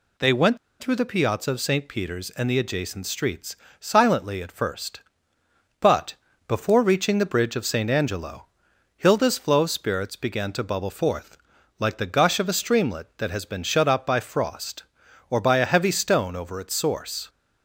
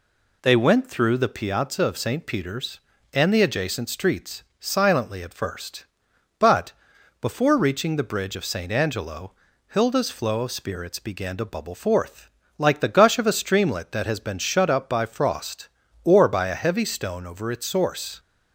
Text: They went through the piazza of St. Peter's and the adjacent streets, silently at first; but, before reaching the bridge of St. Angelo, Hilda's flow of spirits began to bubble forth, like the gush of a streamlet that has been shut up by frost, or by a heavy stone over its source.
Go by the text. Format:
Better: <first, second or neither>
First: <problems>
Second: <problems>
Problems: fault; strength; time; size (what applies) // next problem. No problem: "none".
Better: second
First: pauses between "went" and "through"; slight; at 0.5 s; 0.23 s long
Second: none